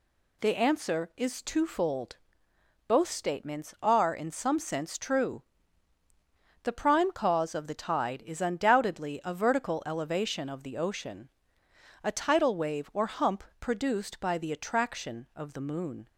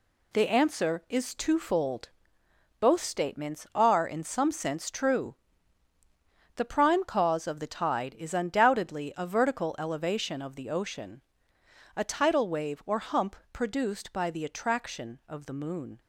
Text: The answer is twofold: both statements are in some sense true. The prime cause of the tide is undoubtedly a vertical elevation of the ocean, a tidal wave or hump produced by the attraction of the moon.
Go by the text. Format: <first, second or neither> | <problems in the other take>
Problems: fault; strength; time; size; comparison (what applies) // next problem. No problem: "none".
first | gets quieter; strong; throughout; 7.5 dB // pauses between "hump" and "produced"; slight; at 13.3 s; 0.16 s long; slight in the first